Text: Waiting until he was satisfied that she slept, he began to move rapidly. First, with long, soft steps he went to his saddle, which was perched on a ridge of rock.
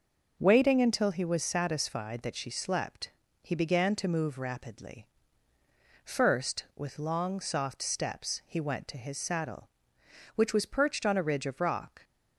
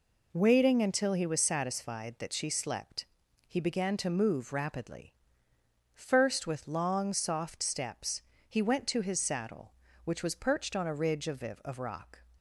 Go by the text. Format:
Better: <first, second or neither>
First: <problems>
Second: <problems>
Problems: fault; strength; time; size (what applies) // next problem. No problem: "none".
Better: first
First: none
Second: pauses between "steps" and "he"; slight; at 8.2 s; 0.26 s long // says "of" twice; at 11.4 s